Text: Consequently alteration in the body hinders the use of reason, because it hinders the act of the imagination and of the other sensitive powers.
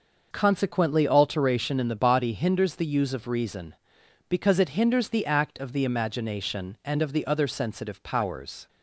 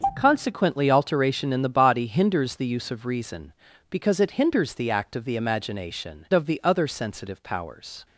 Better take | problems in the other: first | starts louder than the rest; until 1.1 s; 6.5 dB; noticeable in the first // skips "and"; at 6.2 s

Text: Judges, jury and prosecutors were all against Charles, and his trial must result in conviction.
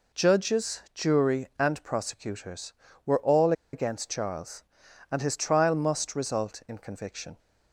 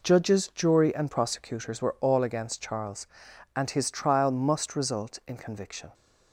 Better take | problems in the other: second | pauses between "all" and "against"; slight; at 3.5 s; 0.21 s long

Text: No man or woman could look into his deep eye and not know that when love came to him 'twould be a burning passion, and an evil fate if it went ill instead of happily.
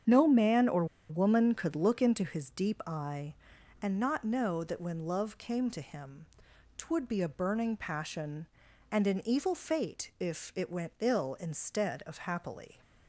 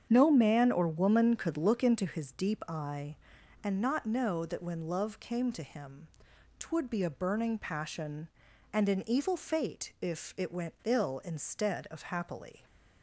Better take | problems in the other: second | starts louder than the rest; strong; until 1.3 s; 8 dB; strong in the second // pauses between "or" and "woman"; slight; at 0.8 s; 0.24 s long // pauses between "him" and "twould"; noticeable; at 6.2 s; 0.50 s long; noticeable in the second

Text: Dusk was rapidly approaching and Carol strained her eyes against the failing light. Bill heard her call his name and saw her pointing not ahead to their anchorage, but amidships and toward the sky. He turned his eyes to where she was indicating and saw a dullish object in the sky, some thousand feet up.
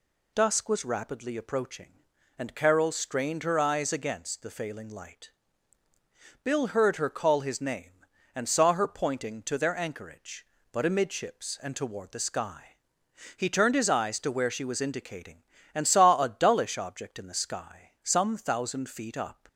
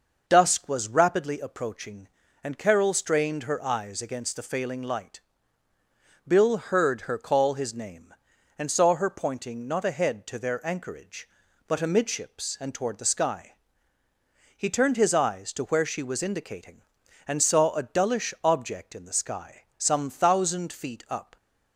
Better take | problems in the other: second | skips "not ahead"; at 9.4 s

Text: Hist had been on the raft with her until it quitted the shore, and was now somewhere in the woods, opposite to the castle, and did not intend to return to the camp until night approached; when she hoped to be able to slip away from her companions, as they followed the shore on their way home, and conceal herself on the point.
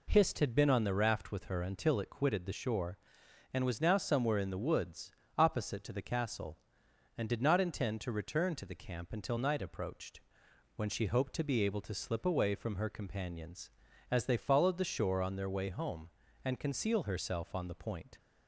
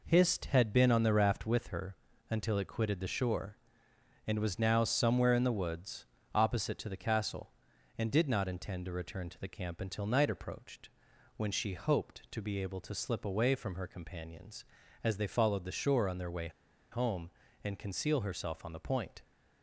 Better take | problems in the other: first | pauses between "her" and "until"; slight; at 1.9 s; 0.34 s long // pauses between "way" and "home"; at 16.4 s; 0.42 s long

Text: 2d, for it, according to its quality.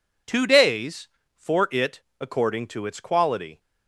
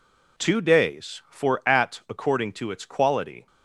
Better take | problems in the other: first | says "at" for "it"; at 1.6 s

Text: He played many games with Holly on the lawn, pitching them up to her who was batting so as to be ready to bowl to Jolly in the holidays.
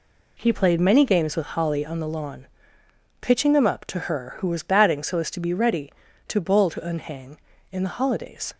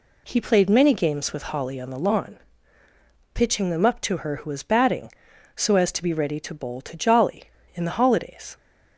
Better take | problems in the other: second | says "Unhang" for "Jolly"; at 6.8 s

